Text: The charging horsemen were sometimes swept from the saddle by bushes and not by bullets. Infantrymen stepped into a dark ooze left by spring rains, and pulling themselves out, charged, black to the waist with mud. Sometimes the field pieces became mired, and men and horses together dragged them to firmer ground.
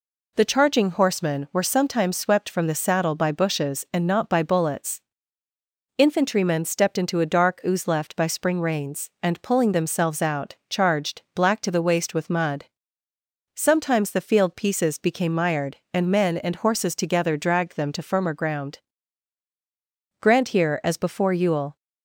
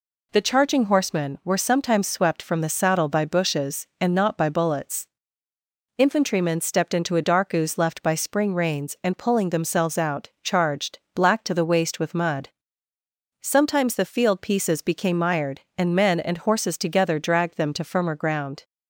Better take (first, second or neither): second